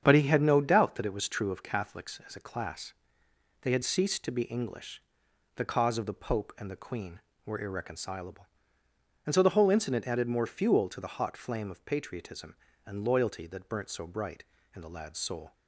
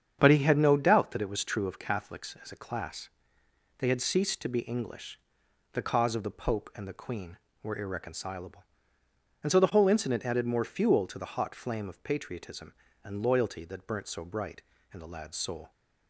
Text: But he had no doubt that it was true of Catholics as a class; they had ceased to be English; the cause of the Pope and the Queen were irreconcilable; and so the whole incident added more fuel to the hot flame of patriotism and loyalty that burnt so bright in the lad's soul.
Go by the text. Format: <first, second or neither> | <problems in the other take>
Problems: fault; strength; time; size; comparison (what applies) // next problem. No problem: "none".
neither | starts louder than the rest; strong; the same in both